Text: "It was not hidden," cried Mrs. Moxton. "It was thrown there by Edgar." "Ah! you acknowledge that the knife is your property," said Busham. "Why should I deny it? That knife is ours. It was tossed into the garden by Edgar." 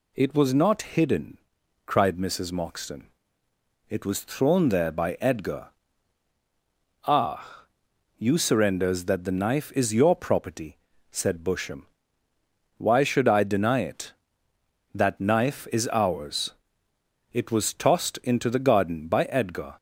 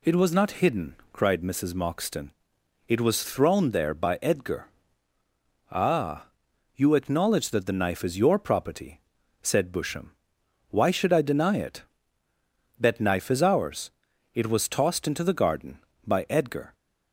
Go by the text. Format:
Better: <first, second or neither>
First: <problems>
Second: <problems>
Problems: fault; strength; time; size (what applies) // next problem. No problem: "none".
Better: second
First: says "surrenders" for "acknowledge"; at 8.3 s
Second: none